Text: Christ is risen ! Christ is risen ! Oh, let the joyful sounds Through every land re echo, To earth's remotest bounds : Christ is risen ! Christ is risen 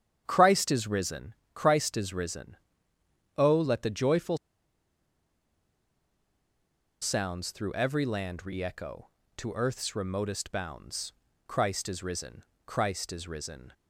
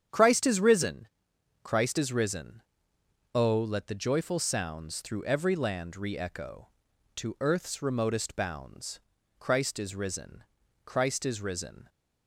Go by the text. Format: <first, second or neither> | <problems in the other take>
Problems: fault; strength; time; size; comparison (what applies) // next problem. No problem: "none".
second | starts louder than the rest; strong; until 1.2 s; 9.5 dB; strong in the second // pauses between "joyful" and "sounds"; strong; at 4.3 s; 2.6 s long